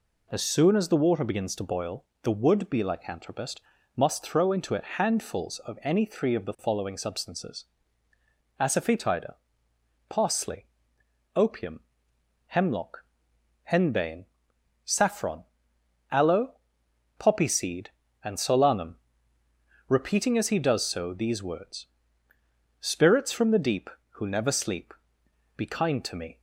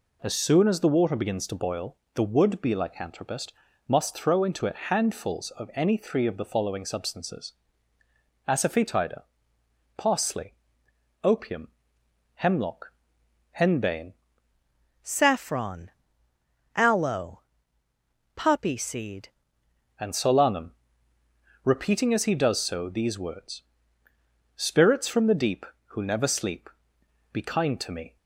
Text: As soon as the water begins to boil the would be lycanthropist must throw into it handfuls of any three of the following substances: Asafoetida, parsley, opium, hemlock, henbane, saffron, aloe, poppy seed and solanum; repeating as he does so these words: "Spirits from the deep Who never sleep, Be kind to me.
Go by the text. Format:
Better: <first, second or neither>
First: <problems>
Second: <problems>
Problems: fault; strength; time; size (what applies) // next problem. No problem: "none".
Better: first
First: pauses between "boil" and "the"; slight; at 2.0 s; 0.18 s long // pauses between "lycanthropist" and "must"; slight; at 3.6 s; 0.34 s long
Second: pauses between "boil" and "the"; slight; at 1.9 s; 0.18 s long // pauses between "lycanthropist" and "must"; slight; at 3.5 s; 0.34 s long // changes voice from "saffron" to "seed"; from 15.0 to 19.2 s; 4.2 s long